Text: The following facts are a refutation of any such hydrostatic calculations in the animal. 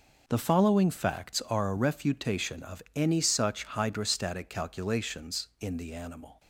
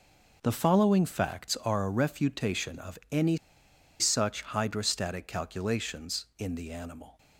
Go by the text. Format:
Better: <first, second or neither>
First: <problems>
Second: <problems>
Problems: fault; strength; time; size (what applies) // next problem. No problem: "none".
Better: first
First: none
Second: pauses between "any" and "such"; noticeable; at 3.3 s; 0.64 s long